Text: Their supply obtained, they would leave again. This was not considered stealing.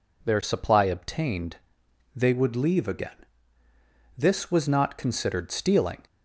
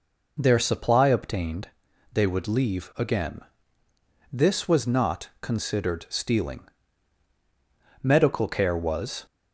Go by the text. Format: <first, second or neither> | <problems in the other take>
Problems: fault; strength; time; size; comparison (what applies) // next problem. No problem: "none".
first | goes on to say "Medical care was"; noticeable; from 8.0 s on; 1.2 s long